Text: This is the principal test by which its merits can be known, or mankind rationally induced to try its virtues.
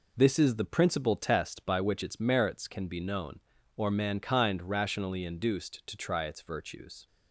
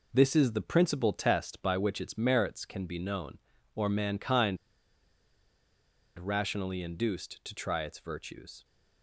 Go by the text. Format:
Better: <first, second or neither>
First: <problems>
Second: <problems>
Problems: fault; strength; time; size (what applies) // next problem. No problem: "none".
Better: first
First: none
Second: pauses between "mankind" and "rationally"; strong; at 4.5 s; 1.6 s long